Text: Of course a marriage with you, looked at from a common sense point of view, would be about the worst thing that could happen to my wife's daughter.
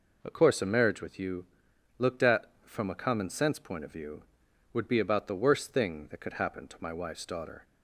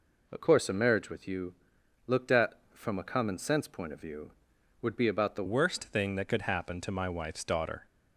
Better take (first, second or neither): first